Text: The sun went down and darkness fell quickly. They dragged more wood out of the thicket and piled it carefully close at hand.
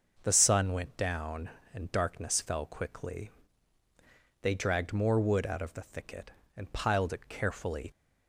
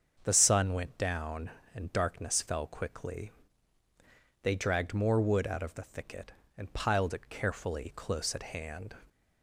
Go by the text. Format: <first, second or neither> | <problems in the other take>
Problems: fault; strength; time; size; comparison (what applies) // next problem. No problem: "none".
second | starts louder than the rest; noticeable; until 1.2 s; 6 dB; also in the second // stops before "close at hand"; at 7.9 s